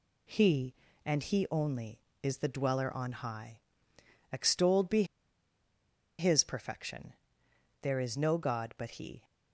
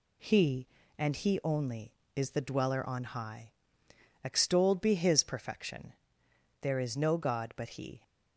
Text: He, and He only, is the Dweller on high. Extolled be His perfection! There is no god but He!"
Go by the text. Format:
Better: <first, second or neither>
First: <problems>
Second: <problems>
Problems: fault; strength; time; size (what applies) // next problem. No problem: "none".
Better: second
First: pauses between "be" and "His"; at 5.0 s; 1.1 s long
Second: none